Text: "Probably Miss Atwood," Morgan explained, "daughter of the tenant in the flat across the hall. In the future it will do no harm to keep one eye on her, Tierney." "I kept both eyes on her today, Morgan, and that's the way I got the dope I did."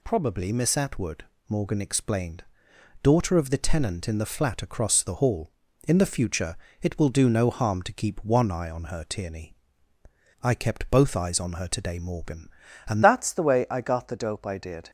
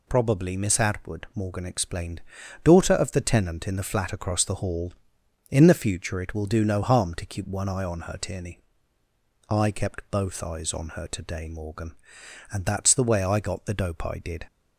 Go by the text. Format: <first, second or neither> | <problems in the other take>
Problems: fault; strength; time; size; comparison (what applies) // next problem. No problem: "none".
second | pauses between "future" and "it"; slight; at 6.5 s; 0.26 s long // changes voice at "that's"; from 13.0 s on; 1.8 s long